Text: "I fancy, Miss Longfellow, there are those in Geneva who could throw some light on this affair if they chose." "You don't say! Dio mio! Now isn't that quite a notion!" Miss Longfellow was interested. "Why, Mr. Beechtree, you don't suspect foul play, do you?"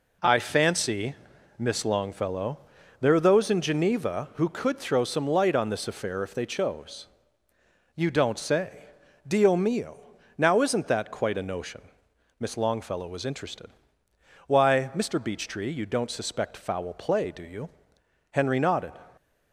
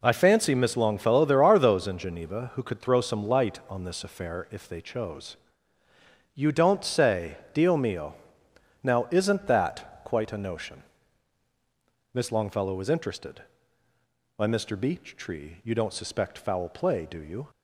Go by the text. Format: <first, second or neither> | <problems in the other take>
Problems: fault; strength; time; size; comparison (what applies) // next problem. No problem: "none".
second | goes on to say "Henry nodded"; noticeable; from 18.3 s on; 0.66 s long